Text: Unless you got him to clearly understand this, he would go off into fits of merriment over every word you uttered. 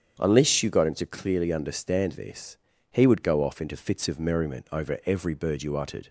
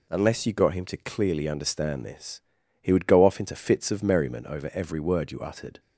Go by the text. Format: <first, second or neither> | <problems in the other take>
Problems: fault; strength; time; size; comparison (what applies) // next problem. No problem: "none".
second | starts louder than the rest; strong; until 1.1 s; 8 dB // says "bird" for "word"; at 5.3 s